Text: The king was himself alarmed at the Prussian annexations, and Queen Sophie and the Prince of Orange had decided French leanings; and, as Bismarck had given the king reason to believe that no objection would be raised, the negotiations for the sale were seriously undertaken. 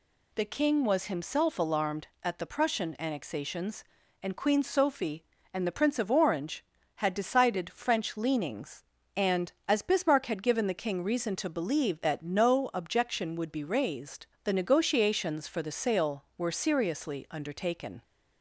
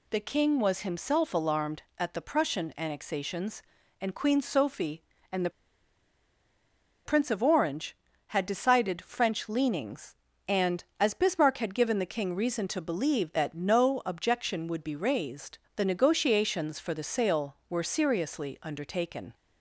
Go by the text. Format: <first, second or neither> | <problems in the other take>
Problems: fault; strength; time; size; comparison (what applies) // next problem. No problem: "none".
first | pauses between "the" and "Prince"; strong; at 5.5 s; 1.5 s long